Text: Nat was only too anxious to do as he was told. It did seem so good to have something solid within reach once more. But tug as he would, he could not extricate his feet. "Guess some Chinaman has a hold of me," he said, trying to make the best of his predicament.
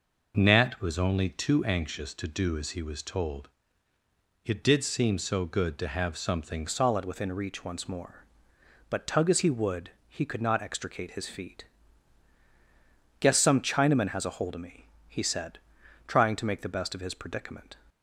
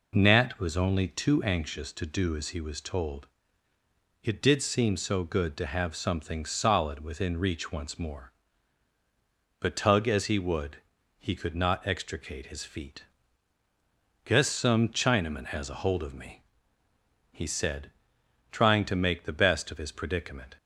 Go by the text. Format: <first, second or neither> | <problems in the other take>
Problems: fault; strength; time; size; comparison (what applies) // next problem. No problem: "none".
second | changes voice at "solid"; from 6.6 s on; 11.1 s long